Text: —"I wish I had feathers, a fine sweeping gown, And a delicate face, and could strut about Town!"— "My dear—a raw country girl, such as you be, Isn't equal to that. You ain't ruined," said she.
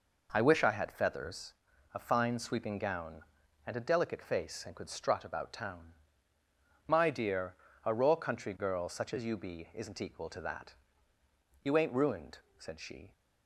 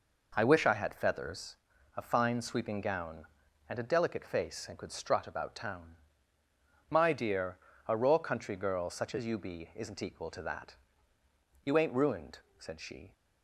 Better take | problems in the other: neither | none

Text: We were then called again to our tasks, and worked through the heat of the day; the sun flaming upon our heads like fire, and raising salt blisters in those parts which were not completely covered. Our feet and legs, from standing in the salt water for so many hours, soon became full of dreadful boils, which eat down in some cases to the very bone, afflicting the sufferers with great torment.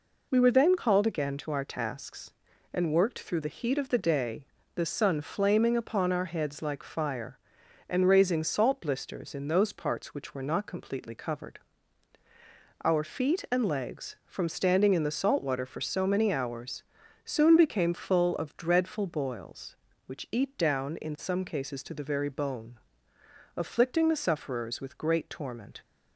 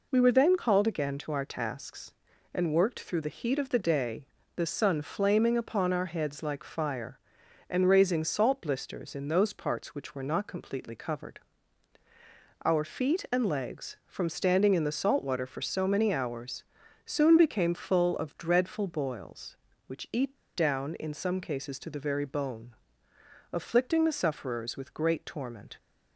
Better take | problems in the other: first | pauses between "eat" and "down"; slight; at 20.3 s; 0.17 s long

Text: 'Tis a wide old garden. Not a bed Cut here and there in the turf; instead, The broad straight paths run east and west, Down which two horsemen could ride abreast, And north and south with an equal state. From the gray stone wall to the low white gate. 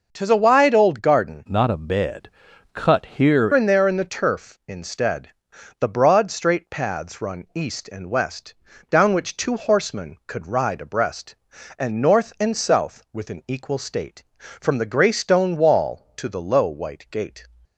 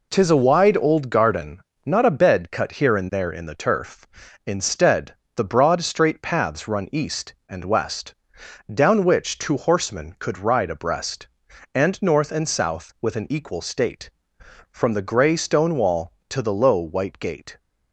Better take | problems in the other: second | changes voice from "Not" to "here"; from 1.4 to 3.4 s; 2.0 s long // pauses between "bed" and "Cut"; at 2.2 s; 0.44 s long

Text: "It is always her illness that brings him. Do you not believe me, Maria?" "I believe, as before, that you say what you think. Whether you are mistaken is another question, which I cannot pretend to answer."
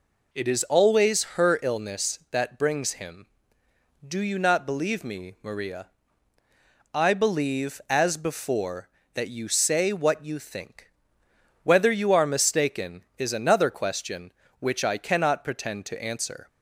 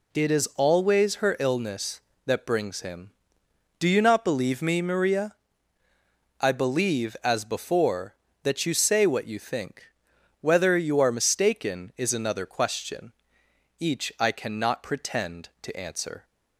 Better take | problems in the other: first | says "each" for "which"; at 13.7 s

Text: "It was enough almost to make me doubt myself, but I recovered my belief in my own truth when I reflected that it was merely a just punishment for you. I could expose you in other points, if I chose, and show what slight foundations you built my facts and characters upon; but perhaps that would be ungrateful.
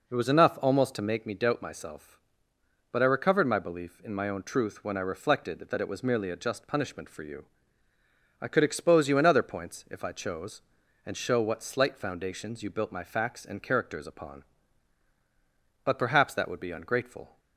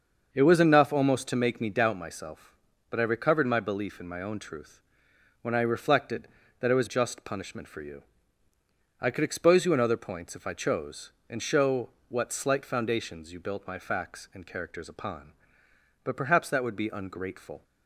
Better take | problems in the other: first | starts louder than the rest; until 1.3 s; 6.5 dB // pauses between "truth" and "when"; noticeable; at 4.7 s; 0.62 s long // skips "merely a"; at 6.8 s // pauses between "show" and "what"; slight; at 11.8 s; 0.20 s long

